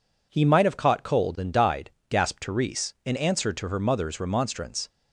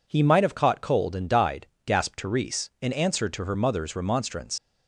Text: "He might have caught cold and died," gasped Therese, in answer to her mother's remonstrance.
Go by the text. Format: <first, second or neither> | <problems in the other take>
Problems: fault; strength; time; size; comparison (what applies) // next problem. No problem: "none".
first | leaves "remonstrance" unfinished; at 4.5 s; 60 ms